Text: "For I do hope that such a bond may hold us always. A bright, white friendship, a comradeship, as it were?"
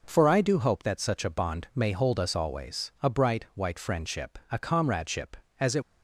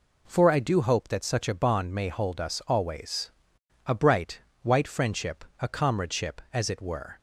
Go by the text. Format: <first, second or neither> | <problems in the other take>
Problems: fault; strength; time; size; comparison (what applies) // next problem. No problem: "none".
second | stops before "were"; at 5.8 s